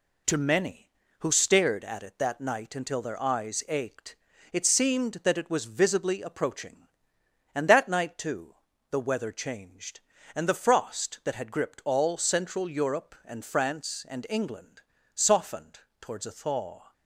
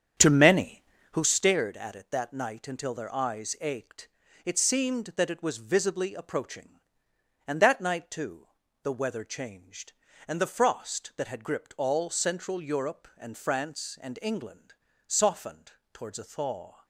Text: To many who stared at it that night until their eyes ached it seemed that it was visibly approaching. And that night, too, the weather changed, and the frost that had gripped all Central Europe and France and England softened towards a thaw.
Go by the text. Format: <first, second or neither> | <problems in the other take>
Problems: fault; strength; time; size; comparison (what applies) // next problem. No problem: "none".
first | starts louder than the rest; strong; until 1.3 s; 8.5 dB // pauses between "ached" and "it"; at 4.0 s; 0.38 s long; also in the first // pauses between "England" and "softened"; slight; at 14.7 s; 0.34 s long; slight in the first // pauses between "softened" and "towards"; slight; at 15.7 s; 0.20 s long; slight in the first